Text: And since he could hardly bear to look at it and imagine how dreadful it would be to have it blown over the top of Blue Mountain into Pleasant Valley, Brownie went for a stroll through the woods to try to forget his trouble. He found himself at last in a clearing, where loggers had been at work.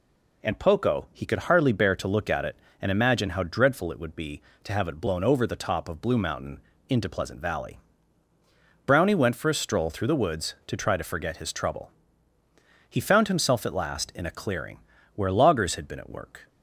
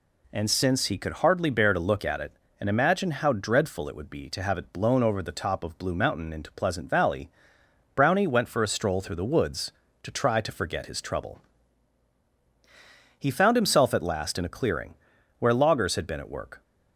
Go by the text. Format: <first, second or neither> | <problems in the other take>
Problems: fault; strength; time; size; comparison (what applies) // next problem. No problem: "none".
second | says "poco" for "since"; at 0.5 s // pauses between "Mountain" and "into"; slight; at 6.5 s; 0.28 s long